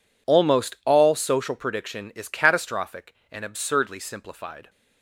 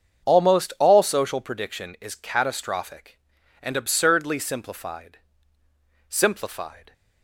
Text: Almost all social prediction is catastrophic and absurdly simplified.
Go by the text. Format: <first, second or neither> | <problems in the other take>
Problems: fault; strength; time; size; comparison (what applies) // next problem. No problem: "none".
first | starts louder than the rest; strong; until 1.3 s; 7 dB // says "simplified" twice; at 6.0 s